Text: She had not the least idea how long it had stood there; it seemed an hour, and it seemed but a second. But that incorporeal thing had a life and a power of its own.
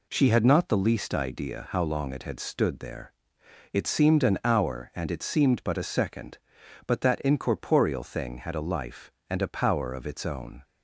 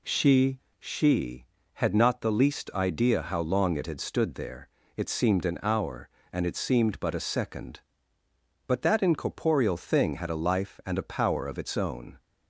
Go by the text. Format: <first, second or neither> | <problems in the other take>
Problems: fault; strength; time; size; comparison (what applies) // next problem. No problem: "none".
first | says "She" twice; at 0.7 s